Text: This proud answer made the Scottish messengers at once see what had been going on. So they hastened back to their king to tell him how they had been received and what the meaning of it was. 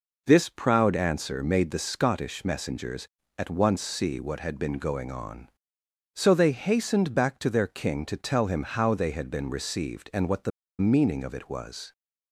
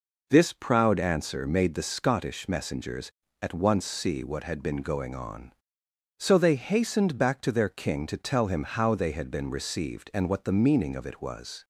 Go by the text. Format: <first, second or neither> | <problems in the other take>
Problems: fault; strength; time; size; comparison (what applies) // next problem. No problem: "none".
second | pauses between "the" and "meaning"; slight; at 10.5 s; 0.29 s long